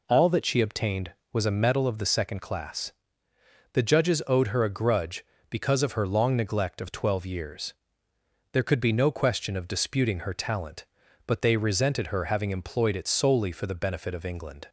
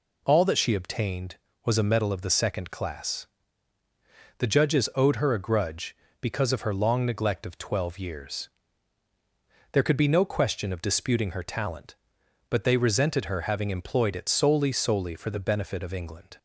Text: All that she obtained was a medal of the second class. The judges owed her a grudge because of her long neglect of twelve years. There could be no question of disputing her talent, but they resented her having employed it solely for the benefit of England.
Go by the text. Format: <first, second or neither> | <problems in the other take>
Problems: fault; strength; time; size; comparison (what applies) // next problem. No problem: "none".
first | says "solely" twice; at 14.7 s